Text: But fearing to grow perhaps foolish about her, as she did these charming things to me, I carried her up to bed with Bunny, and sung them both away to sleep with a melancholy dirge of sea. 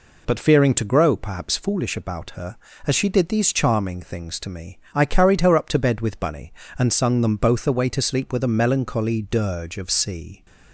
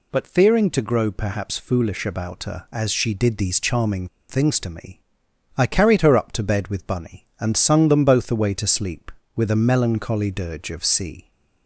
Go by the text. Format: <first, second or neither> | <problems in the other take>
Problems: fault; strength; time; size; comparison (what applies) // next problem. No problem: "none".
first | pauses between "charming" and "things"; slight; at 4.0 s; 0.23 s long